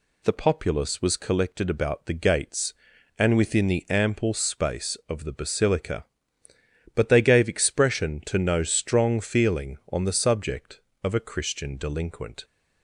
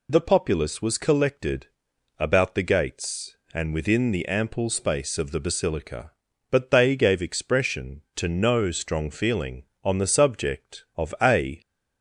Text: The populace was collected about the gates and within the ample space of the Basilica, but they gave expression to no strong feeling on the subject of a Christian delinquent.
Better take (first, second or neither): first